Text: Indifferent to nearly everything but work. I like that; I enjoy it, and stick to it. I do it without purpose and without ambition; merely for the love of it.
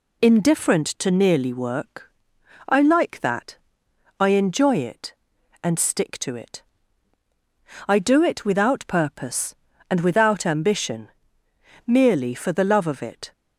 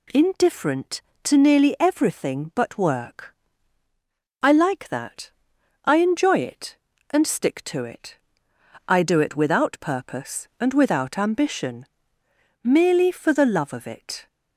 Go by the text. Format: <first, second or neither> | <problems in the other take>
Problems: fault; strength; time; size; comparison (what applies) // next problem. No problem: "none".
second | skips "everything but"; at 1.5 s